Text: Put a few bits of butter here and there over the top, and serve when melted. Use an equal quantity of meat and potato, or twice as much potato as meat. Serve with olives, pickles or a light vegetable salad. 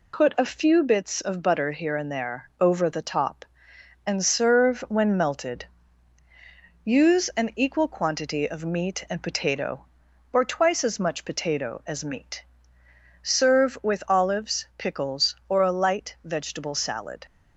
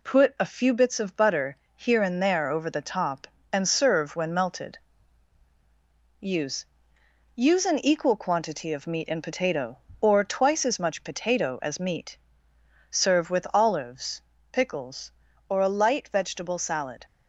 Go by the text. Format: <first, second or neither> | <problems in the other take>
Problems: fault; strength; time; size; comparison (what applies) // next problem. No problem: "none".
first | pauses between "butter" and "here"; slight; at 1.5 s; 0.18 s long // says "Use" twice; at 7.3 s